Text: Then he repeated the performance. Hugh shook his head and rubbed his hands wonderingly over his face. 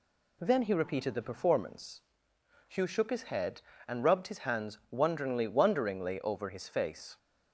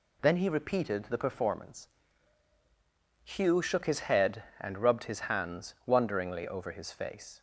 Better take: second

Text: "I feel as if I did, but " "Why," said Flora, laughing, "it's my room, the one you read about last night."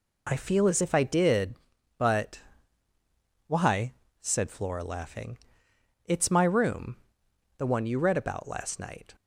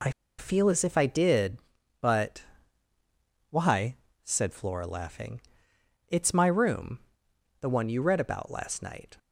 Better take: first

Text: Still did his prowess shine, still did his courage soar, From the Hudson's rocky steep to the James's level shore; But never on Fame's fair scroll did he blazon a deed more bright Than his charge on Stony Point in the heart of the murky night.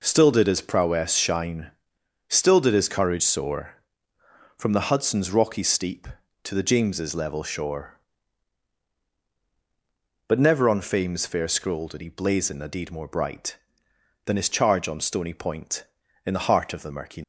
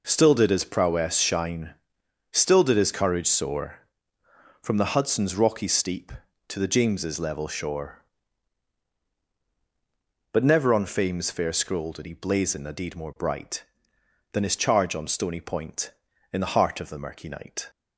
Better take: second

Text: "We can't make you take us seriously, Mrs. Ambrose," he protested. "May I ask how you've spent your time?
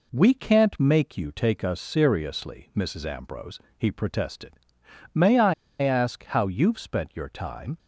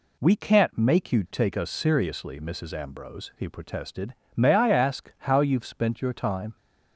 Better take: second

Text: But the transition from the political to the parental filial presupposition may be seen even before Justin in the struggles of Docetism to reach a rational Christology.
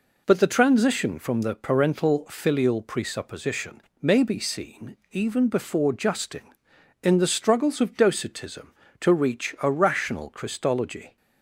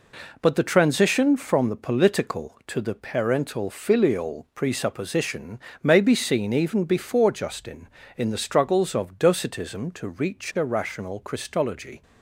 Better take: second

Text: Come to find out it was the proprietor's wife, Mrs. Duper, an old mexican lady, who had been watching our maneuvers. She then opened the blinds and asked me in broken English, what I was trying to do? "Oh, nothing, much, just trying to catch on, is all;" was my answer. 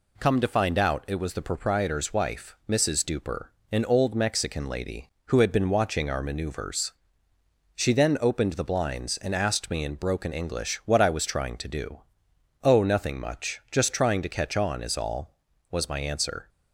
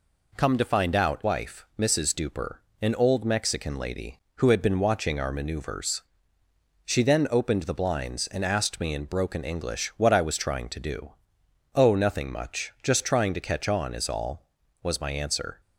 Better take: first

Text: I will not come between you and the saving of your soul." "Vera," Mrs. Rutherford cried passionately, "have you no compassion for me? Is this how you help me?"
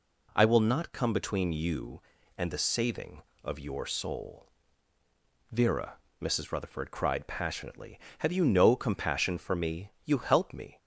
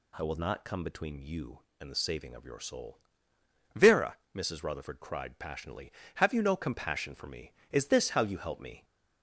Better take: second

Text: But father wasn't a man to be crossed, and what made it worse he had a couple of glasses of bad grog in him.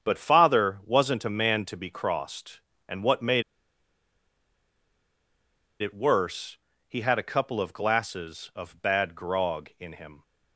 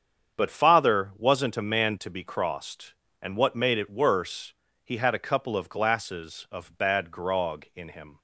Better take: second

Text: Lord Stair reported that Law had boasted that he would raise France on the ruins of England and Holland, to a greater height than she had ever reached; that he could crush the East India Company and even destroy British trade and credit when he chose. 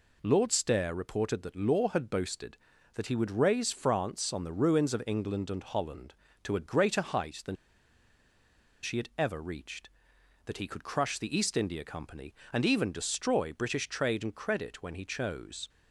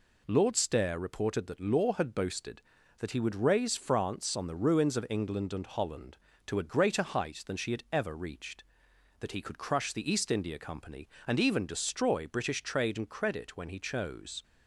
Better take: second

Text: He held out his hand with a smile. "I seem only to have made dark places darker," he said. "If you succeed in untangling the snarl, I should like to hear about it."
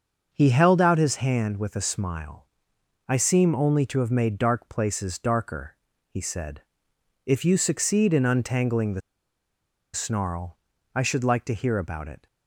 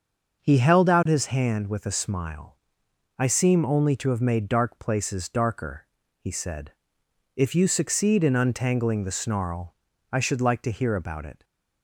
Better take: second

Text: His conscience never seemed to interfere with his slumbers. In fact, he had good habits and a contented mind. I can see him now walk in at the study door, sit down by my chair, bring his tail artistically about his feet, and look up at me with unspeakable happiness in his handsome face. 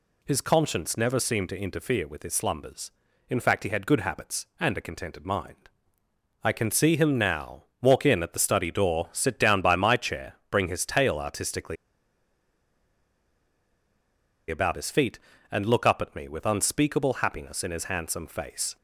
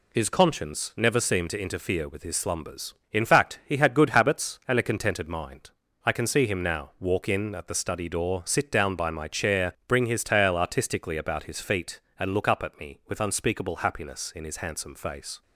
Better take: second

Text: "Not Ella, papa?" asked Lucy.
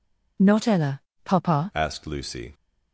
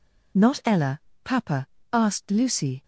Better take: second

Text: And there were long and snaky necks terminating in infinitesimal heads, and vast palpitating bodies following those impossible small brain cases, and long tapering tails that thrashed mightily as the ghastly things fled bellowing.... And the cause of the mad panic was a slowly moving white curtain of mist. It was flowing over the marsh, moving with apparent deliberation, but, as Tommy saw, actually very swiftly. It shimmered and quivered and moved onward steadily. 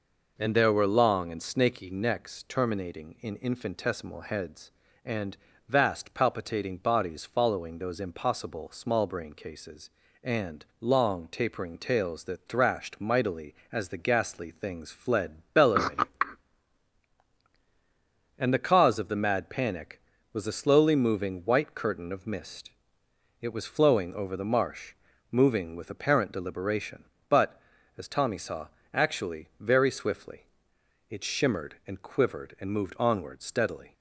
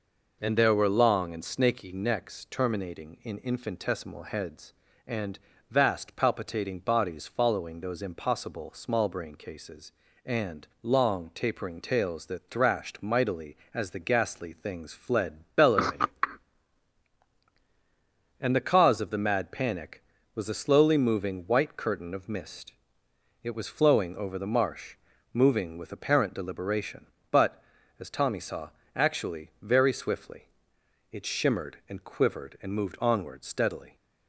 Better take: neither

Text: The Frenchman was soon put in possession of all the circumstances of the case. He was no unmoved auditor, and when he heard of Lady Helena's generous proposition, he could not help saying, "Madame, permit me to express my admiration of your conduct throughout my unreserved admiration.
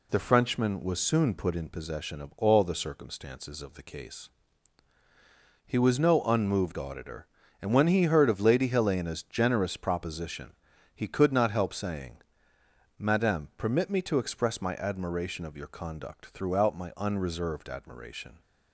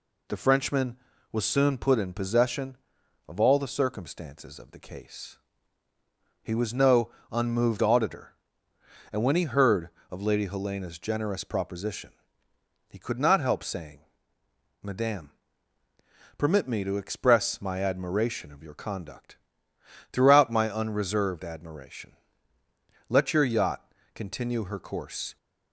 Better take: first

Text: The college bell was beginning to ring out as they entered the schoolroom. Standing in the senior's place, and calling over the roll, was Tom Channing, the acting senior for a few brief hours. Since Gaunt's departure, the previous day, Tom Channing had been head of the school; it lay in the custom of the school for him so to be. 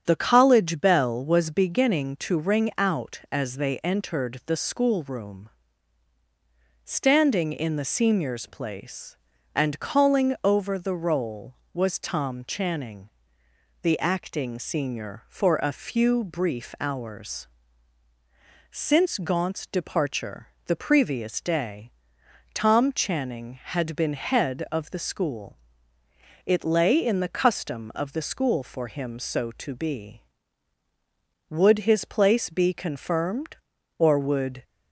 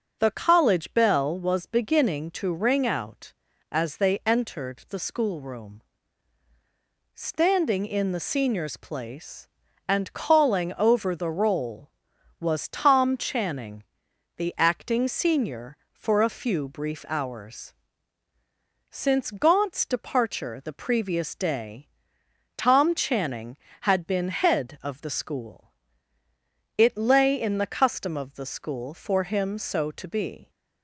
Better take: second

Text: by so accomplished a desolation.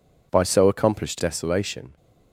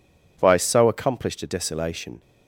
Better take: second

